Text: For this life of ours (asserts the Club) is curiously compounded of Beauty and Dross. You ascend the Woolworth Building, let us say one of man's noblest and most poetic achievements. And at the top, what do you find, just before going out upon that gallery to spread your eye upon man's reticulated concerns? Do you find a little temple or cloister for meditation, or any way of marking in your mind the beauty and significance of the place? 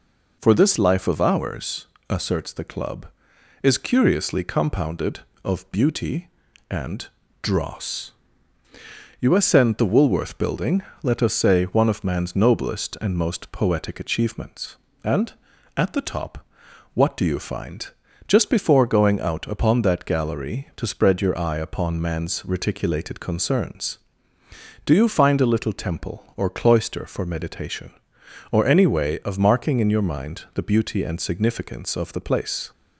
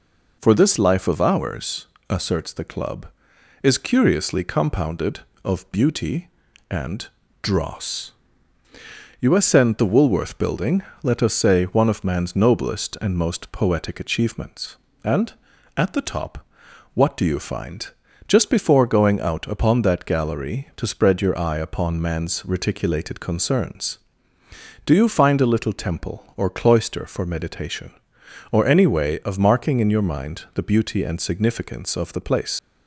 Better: first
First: pauses between "and" and "Dross"; slight; at 7.0 s; 0.36 s long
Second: pauses between "and" and "Dross"; slight; at 7.0 s; 0.36 s long // leaves "place" unfinished; at 32.5 s; 125 ms

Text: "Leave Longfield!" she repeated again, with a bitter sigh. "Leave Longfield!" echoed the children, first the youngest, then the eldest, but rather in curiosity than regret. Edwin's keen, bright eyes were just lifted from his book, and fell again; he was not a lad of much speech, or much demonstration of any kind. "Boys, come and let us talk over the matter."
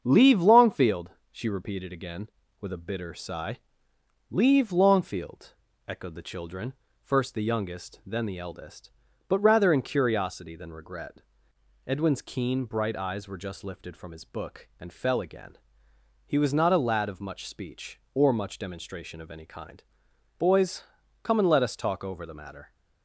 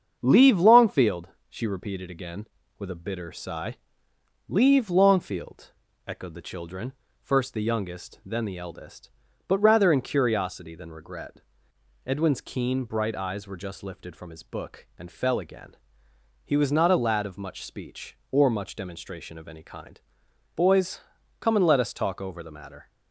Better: neither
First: starts louder than the rest; strong; until 1.0 s; 7 dB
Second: starts louder than the rest; strong; until 1.2 s; 7 dB

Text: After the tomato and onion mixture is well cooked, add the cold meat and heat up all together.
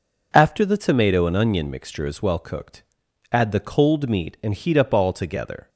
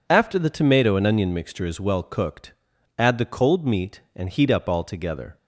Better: neither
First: none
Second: none

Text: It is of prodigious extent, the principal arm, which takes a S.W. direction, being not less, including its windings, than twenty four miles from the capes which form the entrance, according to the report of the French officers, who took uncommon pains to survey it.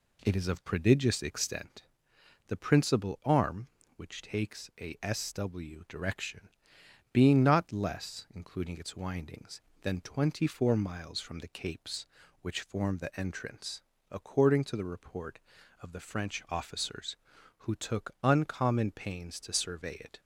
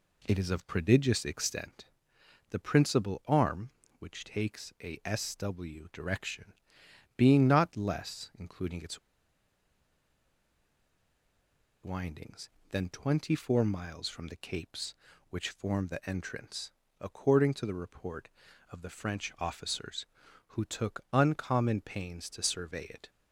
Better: first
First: none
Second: pauses between "its" and "windings"; strong; at 8.9 s; 2.8 s long

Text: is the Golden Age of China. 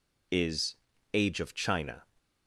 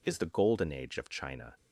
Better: second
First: skips "the Golden"; at 0.9 s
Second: none

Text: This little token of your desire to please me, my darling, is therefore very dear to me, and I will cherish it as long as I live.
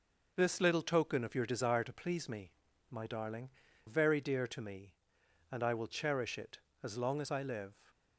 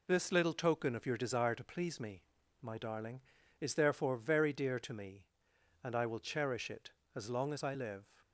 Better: second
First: skips "is therefore"; at 3.6 s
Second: none

